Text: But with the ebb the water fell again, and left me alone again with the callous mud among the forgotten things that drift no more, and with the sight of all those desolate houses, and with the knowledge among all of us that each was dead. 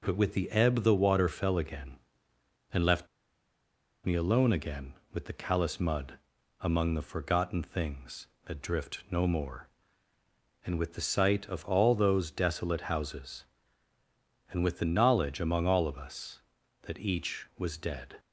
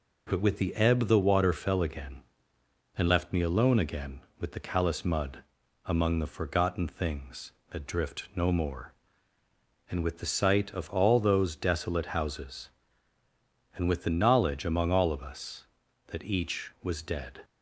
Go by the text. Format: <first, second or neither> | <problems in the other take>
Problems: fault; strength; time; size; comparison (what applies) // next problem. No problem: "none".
second | pauses between "left" and "me"; noticeable; at 3.0 s; 0.98 s long // pauses between "mud" and "among"; at 6.1 s; 0.42 s long; also in the second